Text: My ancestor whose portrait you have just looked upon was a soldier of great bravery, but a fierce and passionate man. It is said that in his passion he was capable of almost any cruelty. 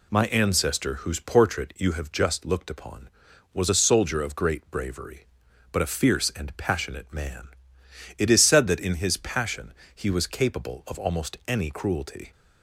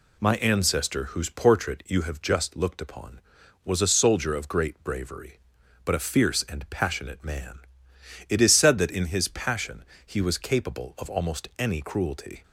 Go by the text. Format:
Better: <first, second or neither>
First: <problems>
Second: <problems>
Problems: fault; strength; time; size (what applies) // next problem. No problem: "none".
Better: neither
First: pauses between "passion" and "he"; slight; at 9.7 s; 0.22 s long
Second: pauses between "passion" and "he"; slight; at 9.8 s; 0.22 s long